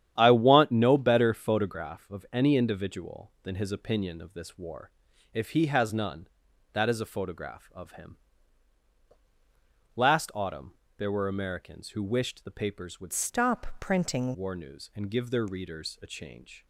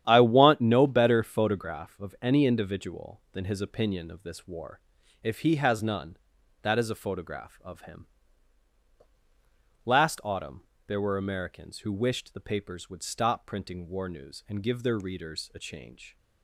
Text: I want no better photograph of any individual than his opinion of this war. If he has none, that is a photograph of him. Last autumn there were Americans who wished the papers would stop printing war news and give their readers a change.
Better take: second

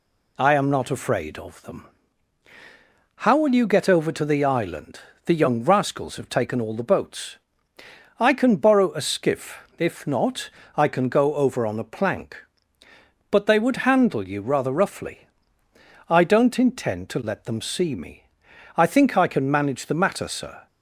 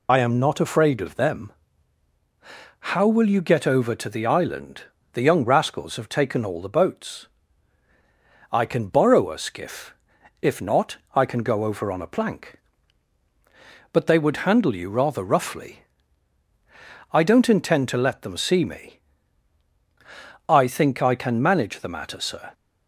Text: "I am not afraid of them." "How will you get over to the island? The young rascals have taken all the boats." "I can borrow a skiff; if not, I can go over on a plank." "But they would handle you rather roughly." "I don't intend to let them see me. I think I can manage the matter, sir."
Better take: first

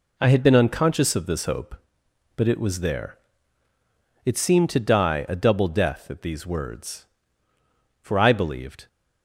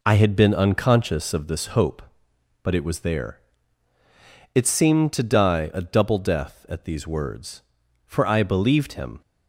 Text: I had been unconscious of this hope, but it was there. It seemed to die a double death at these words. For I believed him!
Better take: second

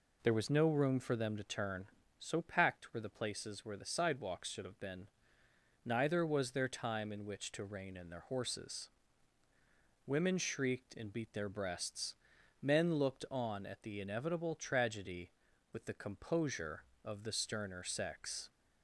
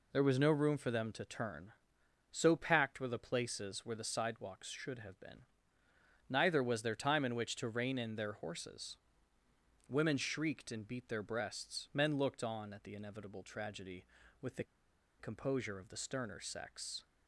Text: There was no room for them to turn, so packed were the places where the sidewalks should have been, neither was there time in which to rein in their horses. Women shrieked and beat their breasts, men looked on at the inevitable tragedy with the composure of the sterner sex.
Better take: first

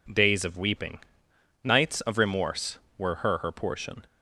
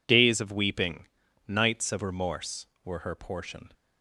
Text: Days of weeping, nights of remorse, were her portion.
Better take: second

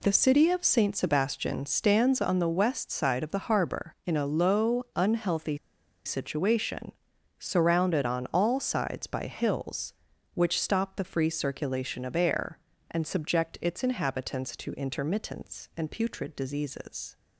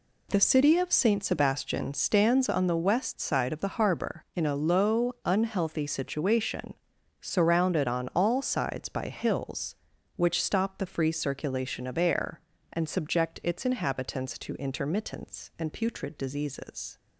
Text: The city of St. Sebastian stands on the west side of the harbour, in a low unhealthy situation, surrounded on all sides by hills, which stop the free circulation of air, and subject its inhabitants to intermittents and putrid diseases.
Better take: second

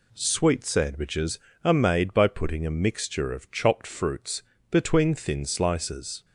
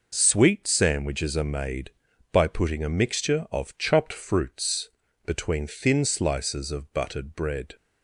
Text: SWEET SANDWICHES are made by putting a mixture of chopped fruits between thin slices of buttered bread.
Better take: second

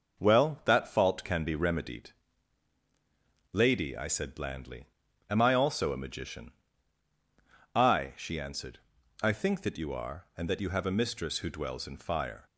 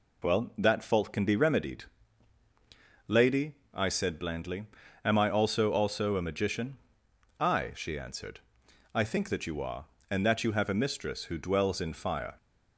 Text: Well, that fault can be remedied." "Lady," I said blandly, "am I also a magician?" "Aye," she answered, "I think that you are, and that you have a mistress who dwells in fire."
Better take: first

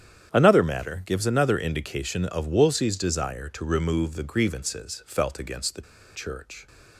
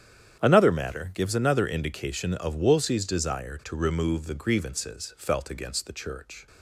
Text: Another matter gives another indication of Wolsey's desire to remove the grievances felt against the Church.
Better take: second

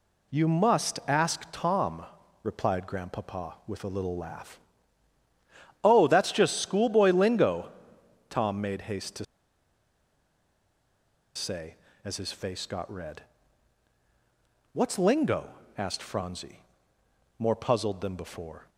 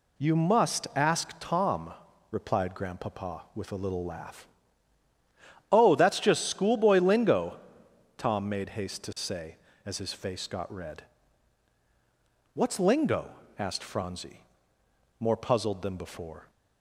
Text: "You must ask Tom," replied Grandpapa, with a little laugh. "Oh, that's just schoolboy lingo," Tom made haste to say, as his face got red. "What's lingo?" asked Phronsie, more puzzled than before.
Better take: second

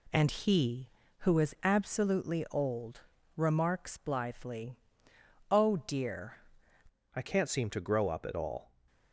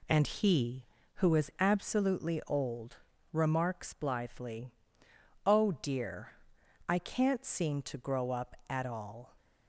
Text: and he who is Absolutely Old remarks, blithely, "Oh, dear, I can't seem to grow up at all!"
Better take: second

